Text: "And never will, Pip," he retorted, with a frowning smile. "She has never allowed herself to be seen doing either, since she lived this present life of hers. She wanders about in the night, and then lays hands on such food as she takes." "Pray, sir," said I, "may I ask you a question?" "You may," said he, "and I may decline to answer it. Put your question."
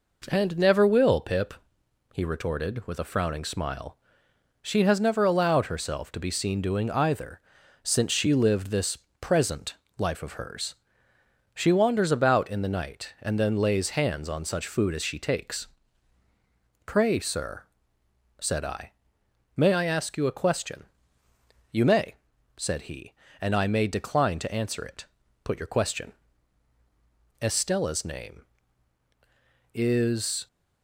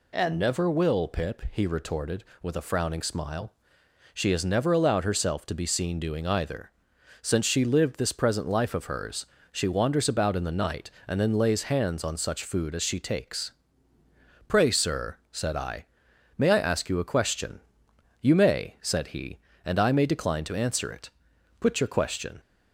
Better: second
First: pauses between "this" and "present"; slight; at 8.9 s; 0.22 s long // pauses between "present" and "life"; slight; at 9.7 s; 0.24 s long // goes on to say "Estella's name Is"; strong; from 27.4 s on; 3.0 s long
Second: none

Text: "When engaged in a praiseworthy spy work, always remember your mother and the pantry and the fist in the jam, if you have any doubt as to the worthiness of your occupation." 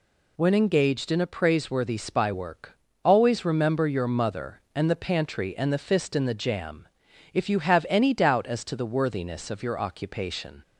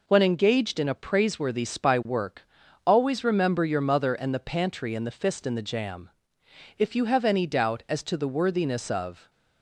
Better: first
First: none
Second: stops before "your occupation"; at 9.2 s

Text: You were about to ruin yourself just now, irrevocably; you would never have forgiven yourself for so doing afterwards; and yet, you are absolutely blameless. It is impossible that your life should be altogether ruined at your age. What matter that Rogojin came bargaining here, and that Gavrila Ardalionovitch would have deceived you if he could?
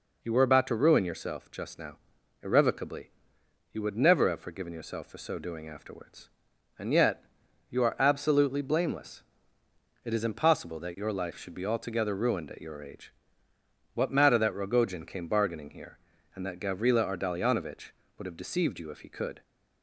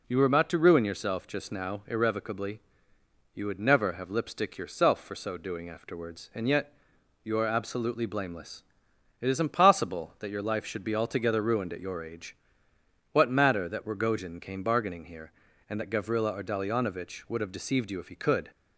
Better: first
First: none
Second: says "lipstick" for "forgiven"; at 4.1 s

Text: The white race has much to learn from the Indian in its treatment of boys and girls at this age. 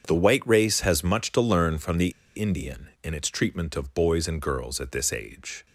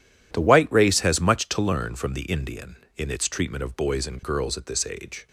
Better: second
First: starts louder than the rest; strong; until 1.0 s; 7.5 dB // pauses between "the" and "Indian"; slight; at 2.0 s; 0.26 s long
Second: none

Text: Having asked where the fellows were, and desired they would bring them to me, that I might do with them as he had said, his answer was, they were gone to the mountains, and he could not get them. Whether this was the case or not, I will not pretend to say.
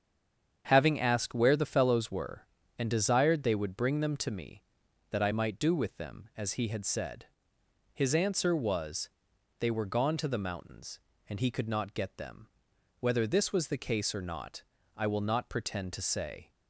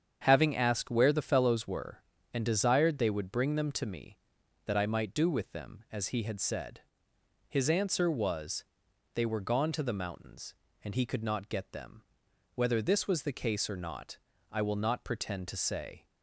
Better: second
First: stays silent before the first word; slight; until 0.6 s; 0.6 s long // starts louder than the rest; strong; until 1.6 s; 8 dB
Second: starts louder than the rest; strong; until 1.2 s; 8 dB

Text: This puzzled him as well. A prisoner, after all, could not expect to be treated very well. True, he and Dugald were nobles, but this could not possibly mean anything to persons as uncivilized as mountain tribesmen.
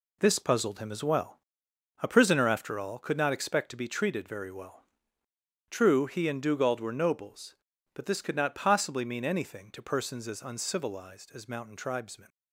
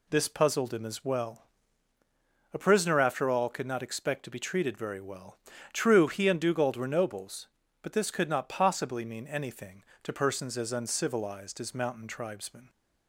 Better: second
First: gets quieter; strong; throughout; 8 dB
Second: none

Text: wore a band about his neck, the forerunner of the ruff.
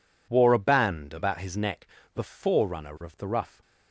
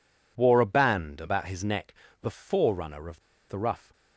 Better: first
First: none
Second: pauses between "of" and "the"; slight; at 3.2 s; 0.27 s long

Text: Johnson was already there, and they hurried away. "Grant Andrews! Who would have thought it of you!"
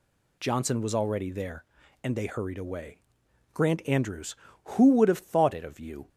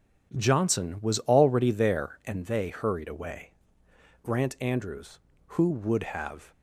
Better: first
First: none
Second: starts louder than the rest; until 1.3 s; 7 dB // stops before "thought it of you"; at 6.5 s

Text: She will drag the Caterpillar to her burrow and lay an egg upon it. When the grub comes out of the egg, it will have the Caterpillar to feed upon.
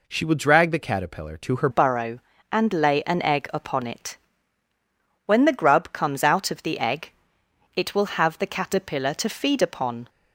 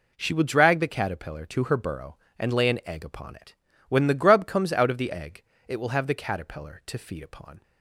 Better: second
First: changes voice at "burrow"; from 1.7 s on; 8.3 s long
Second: none

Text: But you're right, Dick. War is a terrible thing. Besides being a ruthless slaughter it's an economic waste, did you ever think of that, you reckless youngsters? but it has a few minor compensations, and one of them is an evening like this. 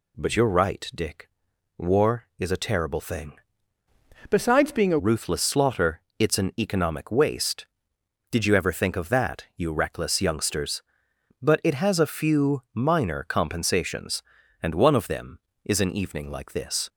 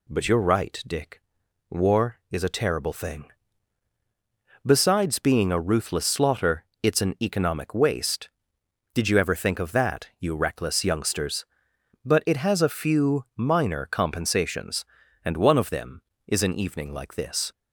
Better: second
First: changes voice from "Besides" to "a"; from 4.2 to 4.9 s; 0.7 s long // pauses between "slaughter" and "it's"; slight; at 6.0 s; 0.16 s long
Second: pauses between "slaughter" and "it's"; slight; at 6.6 s; 0.16 s long

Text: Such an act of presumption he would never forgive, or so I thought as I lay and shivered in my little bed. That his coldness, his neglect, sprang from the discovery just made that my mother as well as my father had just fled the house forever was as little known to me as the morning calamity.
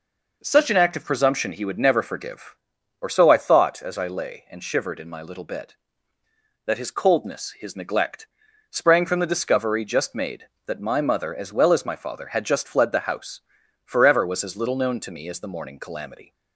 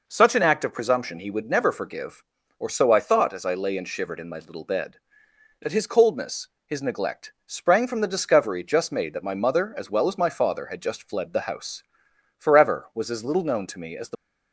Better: first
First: pauses between "house" and "forever"; noticeable; at 13.3 s; 0.46 s long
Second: pauses between "house" and "forever"; noticeable; at 11.8 s; 0.56 s long // stops before "morning calamity"; at 14.1 s

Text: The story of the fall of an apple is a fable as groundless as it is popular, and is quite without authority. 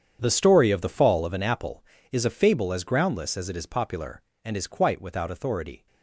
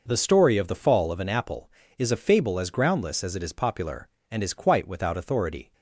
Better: second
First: gets quieter; strong; throughout; 15 dB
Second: none

